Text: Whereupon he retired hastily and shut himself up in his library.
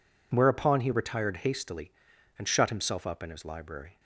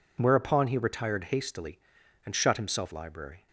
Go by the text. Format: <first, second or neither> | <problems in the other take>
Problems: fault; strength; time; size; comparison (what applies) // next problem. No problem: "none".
first | skips "up in his"; at 2.9 s